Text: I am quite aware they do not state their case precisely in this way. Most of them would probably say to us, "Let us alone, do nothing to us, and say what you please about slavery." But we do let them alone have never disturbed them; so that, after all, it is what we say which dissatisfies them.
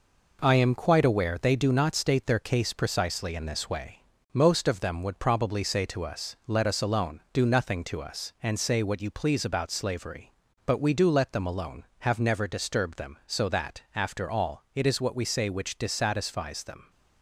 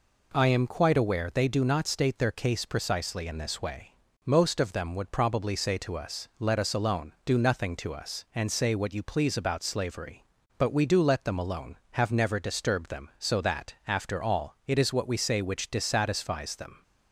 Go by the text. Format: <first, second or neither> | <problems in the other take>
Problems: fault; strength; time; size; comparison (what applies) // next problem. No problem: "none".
second | gets quieter; noticeable; throughout; 5.5 dB